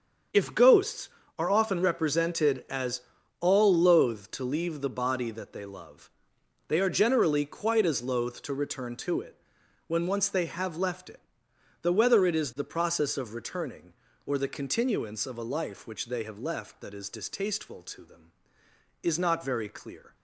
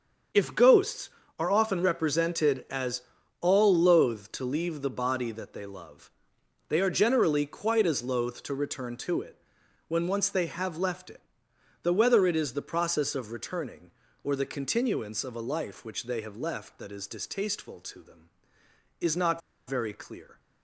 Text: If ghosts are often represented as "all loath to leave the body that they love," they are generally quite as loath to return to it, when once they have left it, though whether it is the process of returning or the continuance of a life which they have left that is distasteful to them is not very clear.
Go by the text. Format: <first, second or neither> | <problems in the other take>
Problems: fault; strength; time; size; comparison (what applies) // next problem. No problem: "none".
first | starts louder than the rest; strong; until 1.6 s; 7.5 dB; strong in the first // pauses between "as" and "all"; at 3.0 s; 0.40 s long; also in the first // pauses between "not" and "very"; slight; at 19.4 s; 0.28 s long